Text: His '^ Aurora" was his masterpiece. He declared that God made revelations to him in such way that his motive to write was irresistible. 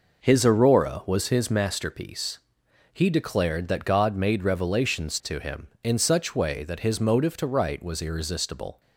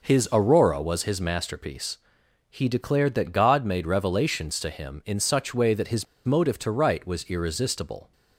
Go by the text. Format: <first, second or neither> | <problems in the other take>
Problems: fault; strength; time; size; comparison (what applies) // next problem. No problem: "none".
first | pauses between "his" and "motive"; slight; at 6.0 s; 0.22 s long